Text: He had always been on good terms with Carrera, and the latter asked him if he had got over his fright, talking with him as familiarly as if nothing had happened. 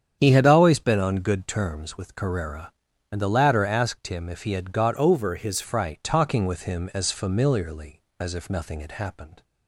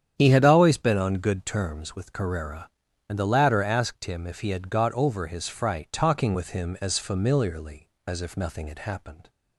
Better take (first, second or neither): second